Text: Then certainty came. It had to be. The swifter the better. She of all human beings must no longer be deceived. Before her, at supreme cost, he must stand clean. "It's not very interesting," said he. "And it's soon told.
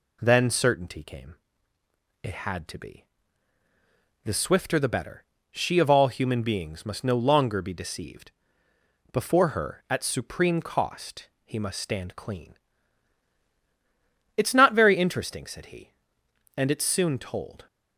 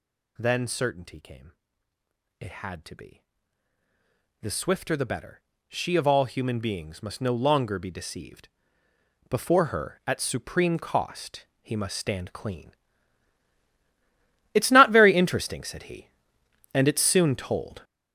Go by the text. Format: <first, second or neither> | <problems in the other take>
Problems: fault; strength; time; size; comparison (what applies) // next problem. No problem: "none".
first | gets louder; strong; throughout; 10 dB